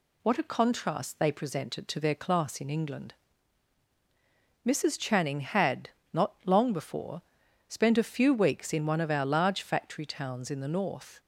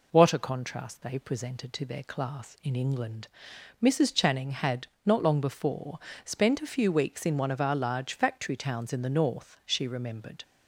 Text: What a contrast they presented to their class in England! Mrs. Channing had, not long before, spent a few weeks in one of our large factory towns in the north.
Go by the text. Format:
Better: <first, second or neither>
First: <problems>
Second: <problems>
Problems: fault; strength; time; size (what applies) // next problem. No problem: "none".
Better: first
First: none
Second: goes on to say "She remembered"; noticeable; from 9.6 s on; 0.78 s long